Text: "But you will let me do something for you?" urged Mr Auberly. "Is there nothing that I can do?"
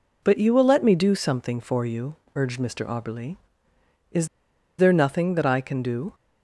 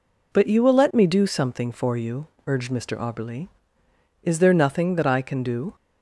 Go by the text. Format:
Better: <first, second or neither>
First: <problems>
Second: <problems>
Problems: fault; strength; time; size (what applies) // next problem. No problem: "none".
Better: second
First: pauses between "Is" and "there"; noticeable; at 4.2 s; 0.50 s long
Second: none